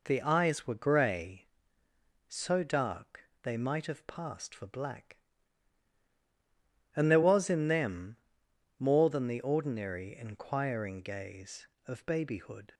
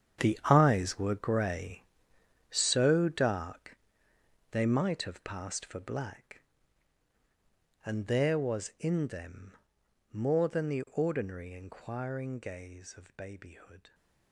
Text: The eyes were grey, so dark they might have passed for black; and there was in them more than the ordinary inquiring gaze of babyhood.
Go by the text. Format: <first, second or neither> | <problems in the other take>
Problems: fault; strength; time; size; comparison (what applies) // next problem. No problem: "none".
first | gets quieter; strong; throughout; 13.5 dB // pauses between "dark" and "they"; noticeable; at 3.7 s; 0.74 s long // pauses between "them" and "more"; noticeable; at 9.5 s; 0.58 s long; noticeable in the first